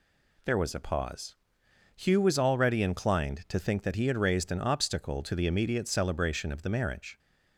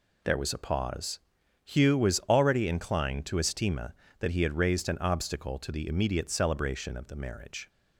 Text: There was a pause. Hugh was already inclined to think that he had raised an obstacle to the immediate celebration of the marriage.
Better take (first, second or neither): first